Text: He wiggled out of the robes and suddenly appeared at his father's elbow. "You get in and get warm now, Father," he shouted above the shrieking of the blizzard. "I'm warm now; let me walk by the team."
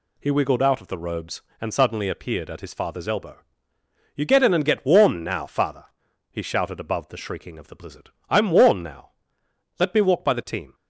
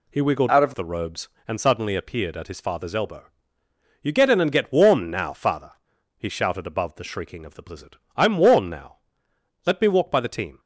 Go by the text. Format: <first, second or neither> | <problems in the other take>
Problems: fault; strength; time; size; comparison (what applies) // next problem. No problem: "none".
first | changes voice from "out" to "of"; from 0.4 to 0.7 s; 0.3 s long